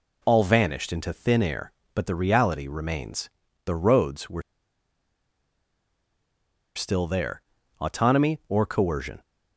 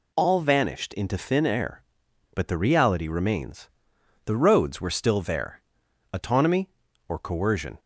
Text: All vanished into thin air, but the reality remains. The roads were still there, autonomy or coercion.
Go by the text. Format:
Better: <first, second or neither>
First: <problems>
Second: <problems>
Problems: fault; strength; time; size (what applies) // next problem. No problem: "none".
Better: second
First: pauses between "were" and "still"; strong; at 4.4 s; 2.3 s long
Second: none